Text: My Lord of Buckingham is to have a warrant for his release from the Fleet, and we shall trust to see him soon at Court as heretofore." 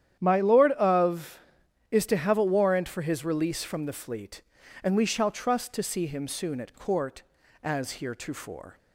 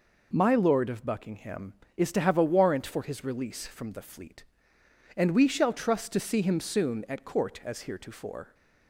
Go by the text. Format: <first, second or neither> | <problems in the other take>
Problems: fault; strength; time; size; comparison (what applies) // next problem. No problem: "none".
second | starts louder than the rest; strong; until 1.2 s; 10 dB // skips "Buckingham"; at 1.6 s